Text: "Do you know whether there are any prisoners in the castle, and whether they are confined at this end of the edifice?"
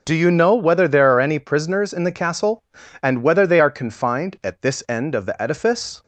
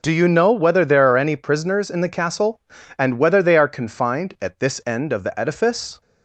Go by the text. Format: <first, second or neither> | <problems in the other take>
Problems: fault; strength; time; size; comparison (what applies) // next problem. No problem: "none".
neither | none